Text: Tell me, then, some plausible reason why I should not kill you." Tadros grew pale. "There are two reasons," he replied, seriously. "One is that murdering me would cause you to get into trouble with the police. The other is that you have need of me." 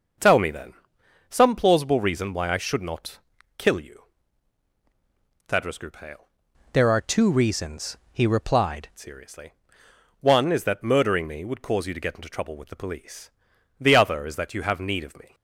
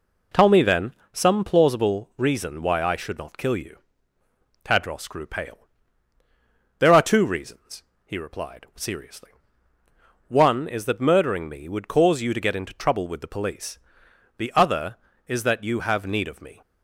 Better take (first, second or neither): second